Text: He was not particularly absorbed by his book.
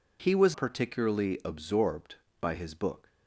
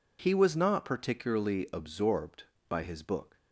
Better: second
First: skips "not"; at 0.5 s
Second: none

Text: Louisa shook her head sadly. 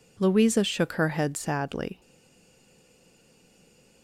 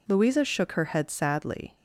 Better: second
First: stays silent after the last word; noticeable; from 2.0 s on; 2.0 s long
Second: none

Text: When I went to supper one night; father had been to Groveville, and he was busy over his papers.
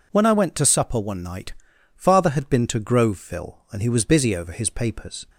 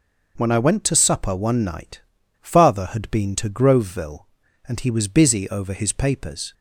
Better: neither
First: none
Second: none

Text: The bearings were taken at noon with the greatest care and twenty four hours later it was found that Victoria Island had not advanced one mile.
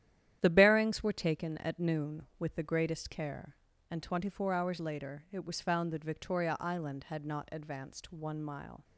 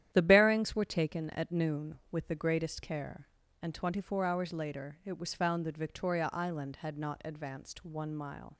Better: neither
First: starts louder than the rest; strong; until 1.4 s; 11 dB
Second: starts louder than the rest; strong; until 1.1 s; 11 dB

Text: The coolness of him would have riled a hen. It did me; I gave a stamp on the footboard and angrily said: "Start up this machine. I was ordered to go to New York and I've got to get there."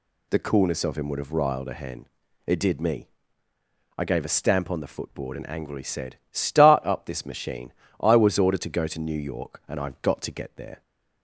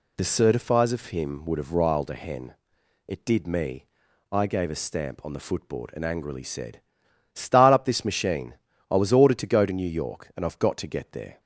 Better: first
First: none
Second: says "certifies" for "coolness"; at 0.2 s

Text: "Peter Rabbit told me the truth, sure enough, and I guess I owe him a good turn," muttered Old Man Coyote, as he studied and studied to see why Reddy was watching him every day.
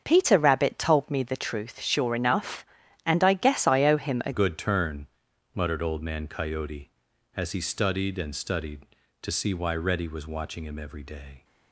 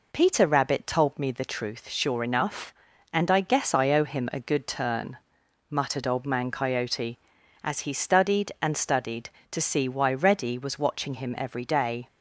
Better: second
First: starts louder than the rest; until 1.0 s; 7 dB // changes voice at "good"; from 4.3 s on; 7.1 s long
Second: none

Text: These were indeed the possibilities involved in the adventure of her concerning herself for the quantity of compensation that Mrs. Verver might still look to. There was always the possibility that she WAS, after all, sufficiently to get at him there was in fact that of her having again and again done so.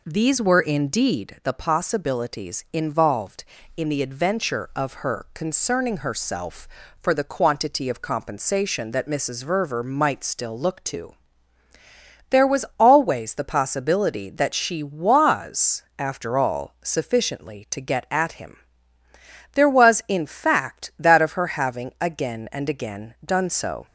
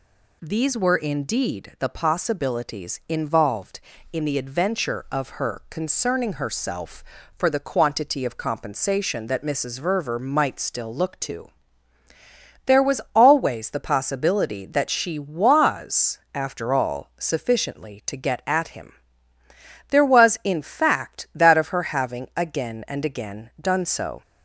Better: second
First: starts louder than the rest; until 1.3 s; 4 dB // pauses between "him" and "there"; noticeable; at 18.5 s; 0.98 s long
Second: pauses between "him" and "there"; noticeable; at 18.9 s; 0.98 s long

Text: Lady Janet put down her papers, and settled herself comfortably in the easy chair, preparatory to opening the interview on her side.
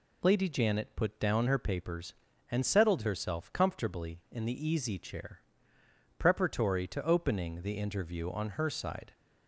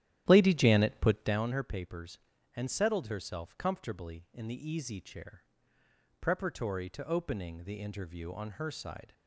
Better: first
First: none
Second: starts louder than the rest; strong; until 1.5 s; 11.5 dB

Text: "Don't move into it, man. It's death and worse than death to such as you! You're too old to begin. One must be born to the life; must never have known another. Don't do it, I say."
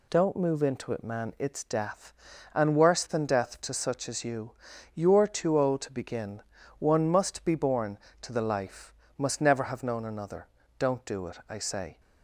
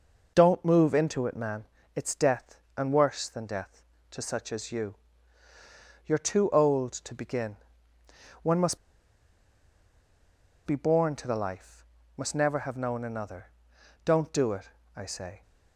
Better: first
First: none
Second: pauses between "must" and "be"; strong; at 8.7 s; 1.8 s long

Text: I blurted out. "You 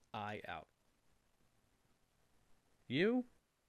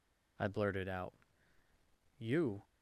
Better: second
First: skips "blurted"; at 0.4 s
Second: none

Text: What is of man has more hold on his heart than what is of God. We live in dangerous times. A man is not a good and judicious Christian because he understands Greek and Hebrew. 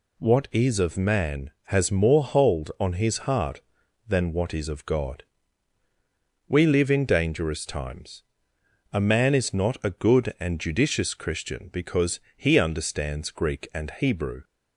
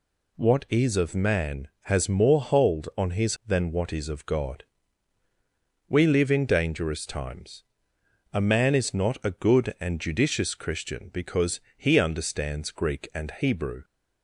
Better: first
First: pauses between "because" and "he"; slight; at 12.2 s; 0.16 s long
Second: skips "heart"; at 3.4 s // pauses between "because" and "he"; slight; at 11.6 s; 0.16 s long

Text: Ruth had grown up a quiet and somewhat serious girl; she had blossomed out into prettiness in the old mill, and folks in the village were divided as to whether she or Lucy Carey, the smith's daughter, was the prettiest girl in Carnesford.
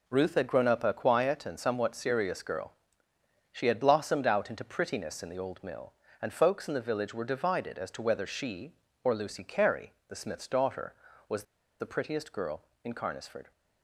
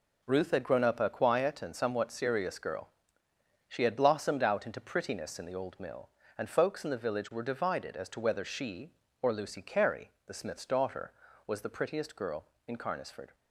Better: second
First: pauses between "was" and "the"; at 11.4 s; 0.37 s long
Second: none

